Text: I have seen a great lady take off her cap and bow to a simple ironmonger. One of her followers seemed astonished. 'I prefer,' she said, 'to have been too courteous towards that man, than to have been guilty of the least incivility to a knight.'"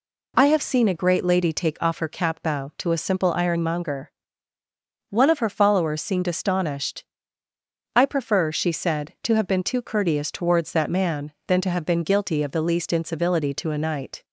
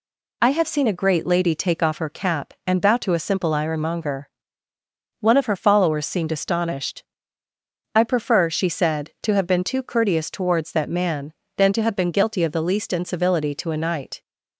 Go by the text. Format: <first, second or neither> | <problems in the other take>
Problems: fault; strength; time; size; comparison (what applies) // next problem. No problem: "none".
second | skips "and"; at 2.4 s